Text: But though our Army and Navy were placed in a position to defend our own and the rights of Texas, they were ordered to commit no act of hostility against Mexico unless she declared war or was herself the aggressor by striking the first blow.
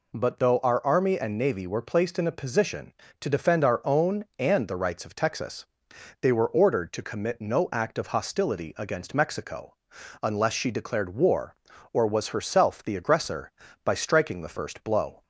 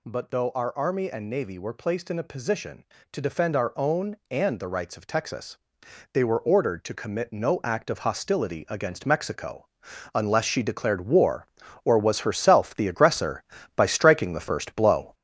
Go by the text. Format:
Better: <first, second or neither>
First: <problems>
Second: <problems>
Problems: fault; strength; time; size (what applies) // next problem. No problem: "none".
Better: first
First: pauses between "Mexico" and "unless"; noticeable; at 9.7 s; 0.48 s long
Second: gets louder; noticeable; throughout; 6 dB // pauses between "Mexico" and "unless"; noticeable; at 9.6 s; 0.48 s long